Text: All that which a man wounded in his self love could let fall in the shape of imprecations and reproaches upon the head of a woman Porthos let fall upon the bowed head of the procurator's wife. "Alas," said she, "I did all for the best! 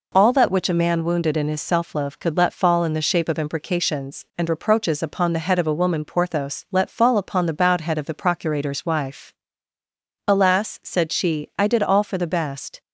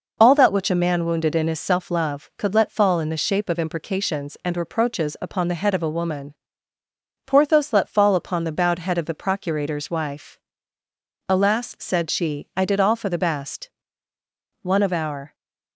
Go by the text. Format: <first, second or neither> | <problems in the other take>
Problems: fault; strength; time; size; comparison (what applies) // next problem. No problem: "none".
first | pauses between "woman" and "Porthos"; noticeable; at 6.3 s; 0.92 s long // goes on to say "One of our"; noticeable; from 14.6 s on; 0.72 s long